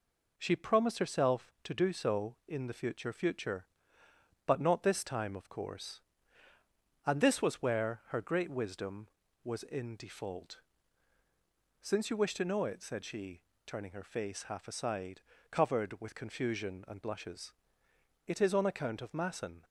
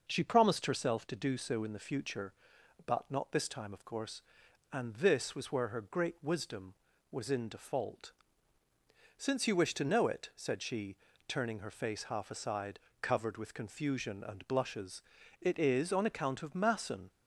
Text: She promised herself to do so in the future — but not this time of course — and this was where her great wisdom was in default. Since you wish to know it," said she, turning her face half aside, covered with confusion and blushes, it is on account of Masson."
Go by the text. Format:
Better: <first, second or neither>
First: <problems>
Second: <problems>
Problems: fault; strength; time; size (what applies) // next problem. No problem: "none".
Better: second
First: says "future" twice; at 3.1 s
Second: none